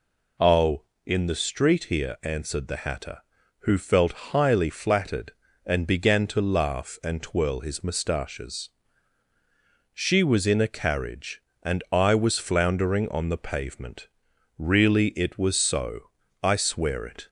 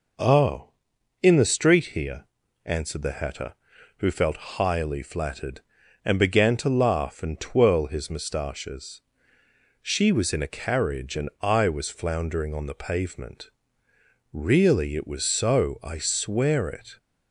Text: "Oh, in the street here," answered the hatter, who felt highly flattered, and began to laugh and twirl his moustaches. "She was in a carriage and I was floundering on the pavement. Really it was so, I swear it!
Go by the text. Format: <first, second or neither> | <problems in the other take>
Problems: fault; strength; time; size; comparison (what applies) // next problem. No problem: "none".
neither | none